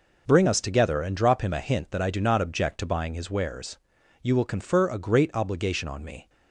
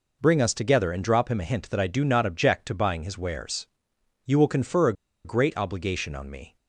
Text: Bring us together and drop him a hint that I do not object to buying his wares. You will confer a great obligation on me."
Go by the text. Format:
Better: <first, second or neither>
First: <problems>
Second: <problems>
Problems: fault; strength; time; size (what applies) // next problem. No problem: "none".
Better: first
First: none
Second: pauses between "a" and "great"; slight; at 4.9 s; 0.32 s long